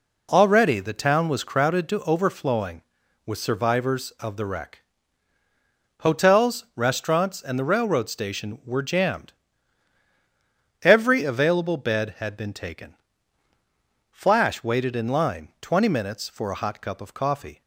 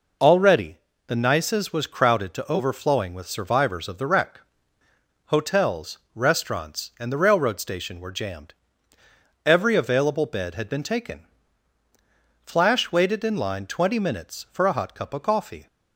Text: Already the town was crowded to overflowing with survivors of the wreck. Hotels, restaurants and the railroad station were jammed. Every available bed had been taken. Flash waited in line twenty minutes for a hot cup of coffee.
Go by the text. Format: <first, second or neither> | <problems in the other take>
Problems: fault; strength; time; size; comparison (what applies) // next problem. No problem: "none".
first | pauses between "Already" and "the"; slight; at 0.7 s; 0.30 s long // says "nices" for "town"; at 1.1 s